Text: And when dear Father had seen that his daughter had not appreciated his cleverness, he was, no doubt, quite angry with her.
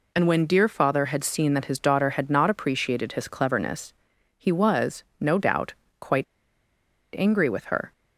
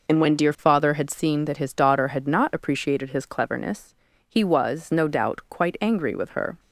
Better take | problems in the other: second | pauses between "quite" and "angry"; noticeable; at 6.2 s; 0.92 s long

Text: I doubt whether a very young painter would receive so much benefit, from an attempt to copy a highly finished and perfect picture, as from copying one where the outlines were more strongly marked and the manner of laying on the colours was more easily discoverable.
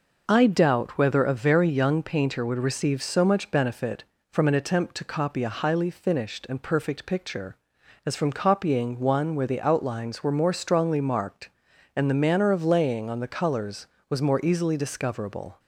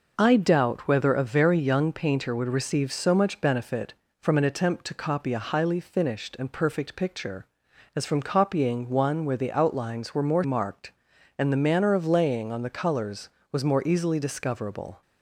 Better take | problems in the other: first | skips "strongly"; at 10.4 s

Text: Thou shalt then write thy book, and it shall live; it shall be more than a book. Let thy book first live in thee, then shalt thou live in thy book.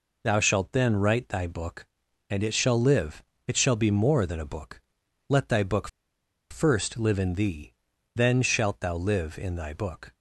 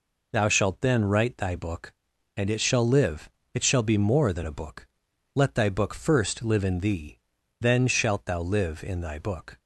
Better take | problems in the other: second | pauses between "book" and "first"; noticeable; at 5.8 s; 0.62 s long

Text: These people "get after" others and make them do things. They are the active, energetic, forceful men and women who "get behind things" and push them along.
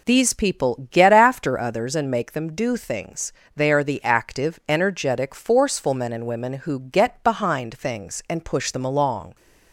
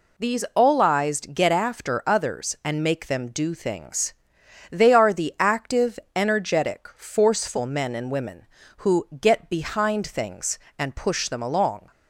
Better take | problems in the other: first | says "olized" for "people"; at 0.5 s

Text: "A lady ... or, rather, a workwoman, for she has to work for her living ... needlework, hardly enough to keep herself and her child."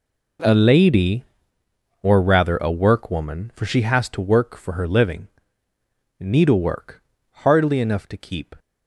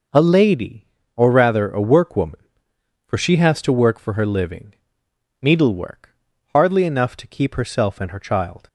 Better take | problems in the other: second | stops before "herself and her child"; at 8.5 s

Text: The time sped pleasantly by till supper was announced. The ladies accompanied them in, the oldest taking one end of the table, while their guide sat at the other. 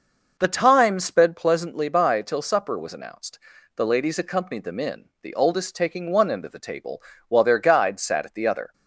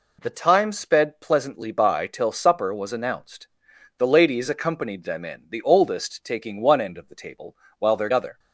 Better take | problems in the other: first | skips "guide sat at the"; at 8.1 s

